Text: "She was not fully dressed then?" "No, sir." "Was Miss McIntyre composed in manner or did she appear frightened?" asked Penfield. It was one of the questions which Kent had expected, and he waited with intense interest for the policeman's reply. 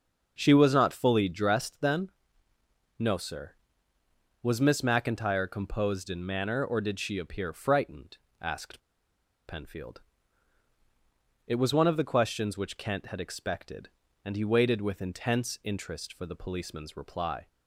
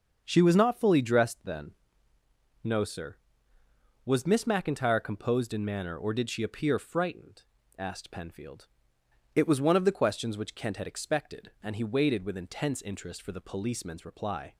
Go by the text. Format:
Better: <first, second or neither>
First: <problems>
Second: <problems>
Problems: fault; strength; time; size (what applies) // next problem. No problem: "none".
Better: second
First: starts louder than the rest; noticeable; until 1.3 s; 6 dB // pauses between "asked" and "Penfield"; noticeable; at 8.7 s; 0.68 s long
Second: starts louder than the rest; until 1.2 s; 7 dB